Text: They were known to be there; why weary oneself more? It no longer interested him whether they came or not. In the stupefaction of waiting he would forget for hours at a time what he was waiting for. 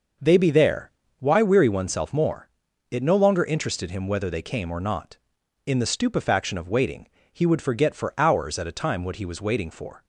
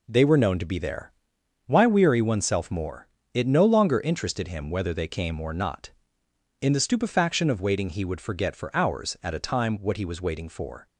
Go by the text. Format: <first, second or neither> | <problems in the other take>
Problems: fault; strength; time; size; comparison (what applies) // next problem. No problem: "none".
second | skips "were known to"; at 0.3 s // pauses between "waiting" and "he"; slight; at 7.0 s; 0.22 s long